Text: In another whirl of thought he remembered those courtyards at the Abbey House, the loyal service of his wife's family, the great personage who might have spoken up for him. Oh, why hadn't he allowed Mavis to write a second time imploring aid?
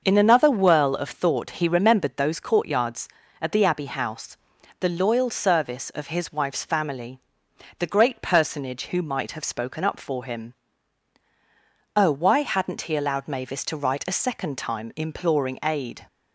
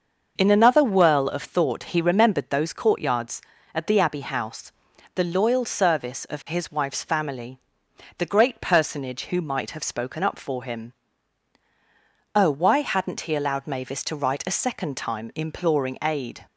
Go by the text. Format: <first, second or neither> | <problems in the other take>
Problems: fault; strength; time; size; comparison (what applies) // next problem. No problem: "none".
neither | starts louder than the rest; the same in both